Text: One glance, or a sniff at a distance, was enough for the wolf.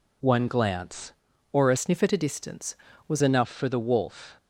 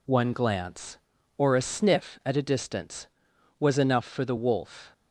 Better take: second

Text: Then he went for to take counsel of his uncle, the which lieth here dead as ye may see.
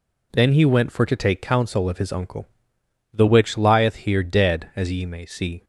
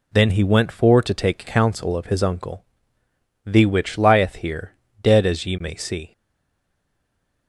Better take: first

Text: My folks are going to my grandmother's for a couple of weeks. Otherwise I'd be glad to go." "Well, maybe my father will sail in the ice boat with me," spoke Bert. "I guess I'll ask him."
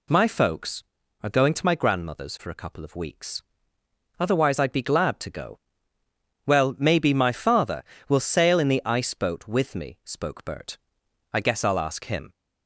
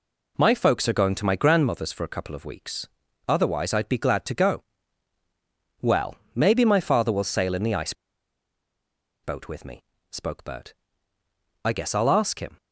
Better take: first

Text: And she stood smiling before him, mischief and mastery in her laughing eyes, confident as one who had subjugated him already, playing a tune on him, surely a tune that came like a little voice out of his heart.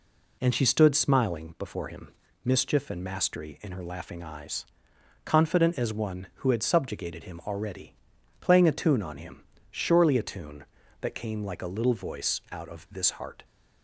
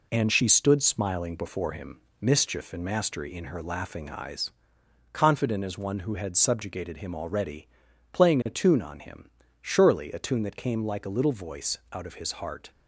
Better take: second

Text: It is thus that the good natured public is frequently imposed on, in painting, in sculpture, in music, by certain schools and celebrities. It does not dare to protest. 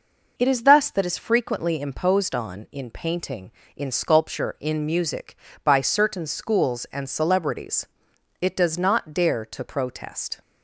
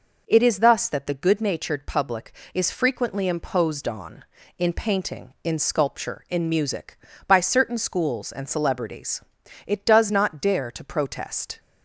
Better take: second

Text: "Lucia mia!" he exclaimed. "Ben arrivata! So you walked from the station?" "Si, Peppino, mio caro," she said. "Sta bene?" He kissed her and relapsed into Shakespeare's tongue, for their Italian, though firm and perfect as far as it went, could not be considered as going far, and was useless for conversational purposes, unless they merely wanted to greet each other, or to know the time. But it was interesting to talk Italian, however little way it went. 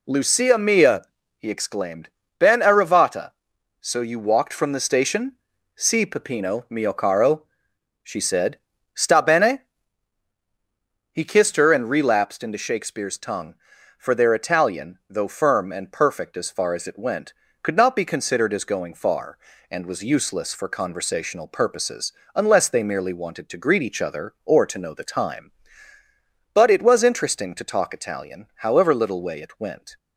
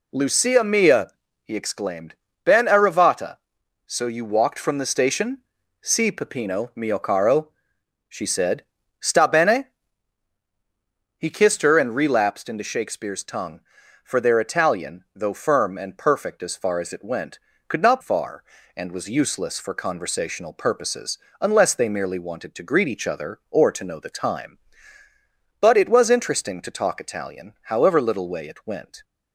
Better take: first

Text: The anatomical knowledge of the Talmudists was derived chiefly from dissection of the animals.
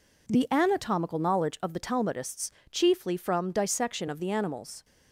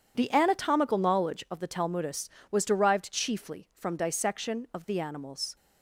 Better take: second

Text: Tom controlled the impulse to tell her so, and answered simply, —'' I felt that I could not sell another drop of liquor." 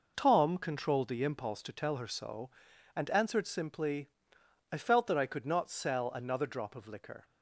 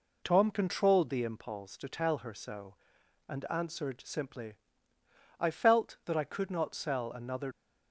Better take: first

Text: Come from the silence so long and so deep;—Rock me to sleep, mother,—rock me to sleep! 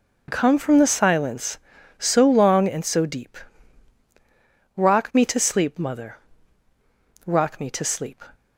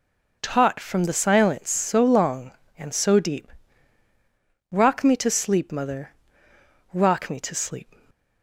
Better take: first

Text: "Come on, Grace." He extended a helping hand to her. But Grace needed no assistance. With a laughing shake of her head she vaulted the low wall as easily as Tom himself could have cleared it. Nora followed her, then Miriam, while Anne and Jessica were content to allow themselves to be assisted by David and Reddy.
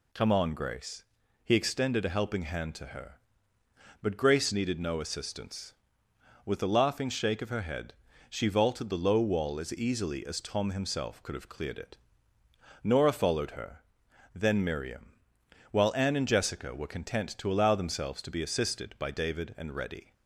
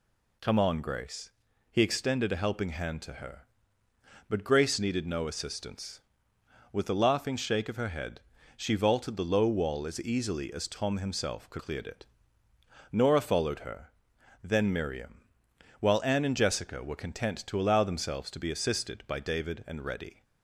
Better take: first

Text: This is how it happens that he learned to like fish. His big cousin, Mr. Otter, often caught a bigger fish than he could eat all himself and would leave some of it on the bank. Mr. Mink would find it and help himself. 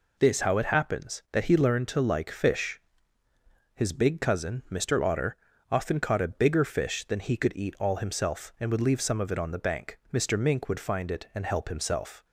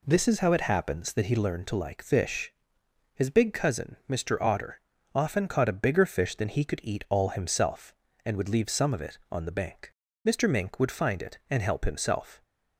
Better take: second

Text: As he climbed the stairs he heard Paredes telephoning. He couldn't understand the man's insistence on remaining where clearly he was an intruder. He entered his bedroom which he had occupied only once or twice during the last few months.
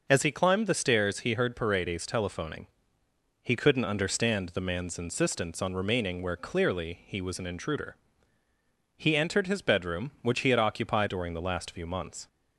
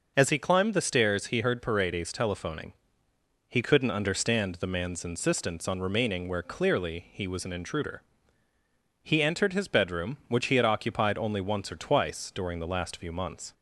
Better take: second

